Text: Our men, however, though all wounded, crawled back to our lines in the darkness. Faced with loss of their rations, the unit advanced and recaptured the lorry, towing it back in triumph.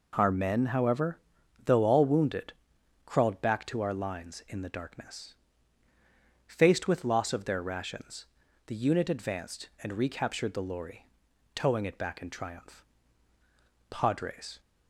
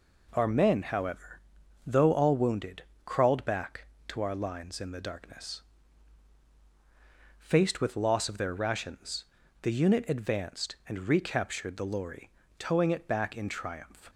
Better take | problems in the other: second | goes on to say "Padres"; noticeable; from 13.8 s on; 0.70 s long

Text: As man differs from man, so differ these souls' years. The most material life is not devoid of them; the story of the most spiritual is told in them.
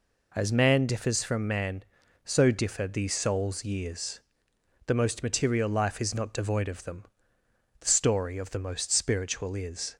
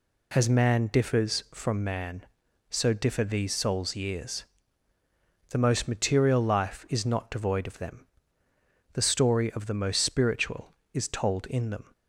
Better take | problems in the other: second | stops before "told in them"; at 9.9 s

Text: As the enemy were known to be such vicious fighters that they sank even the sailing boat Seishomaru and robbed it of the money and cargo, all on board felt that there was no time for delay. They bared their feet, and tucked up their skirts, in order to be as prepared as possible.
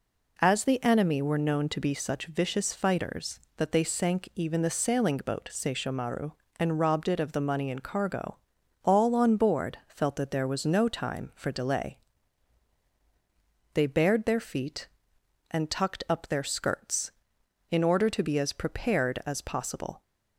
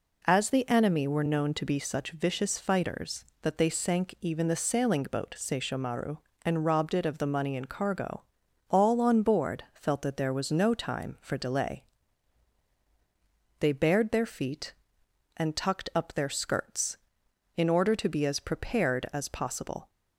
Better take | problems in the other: neither | none

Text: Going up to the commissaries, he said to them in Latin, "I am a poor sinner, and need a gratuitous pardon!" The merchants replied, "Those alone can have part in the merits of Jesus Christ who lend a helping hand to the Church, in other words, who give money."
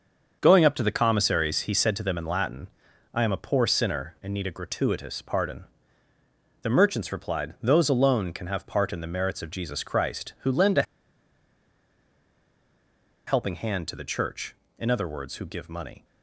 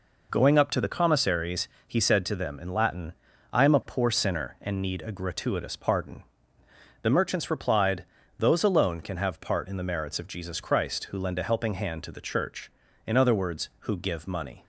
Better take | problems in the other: second | starts louder than the rest; until 1.4 s; 6.5 dB // pauses between "a" and "helping"; strong; at 10.8 s; 2.4 s long

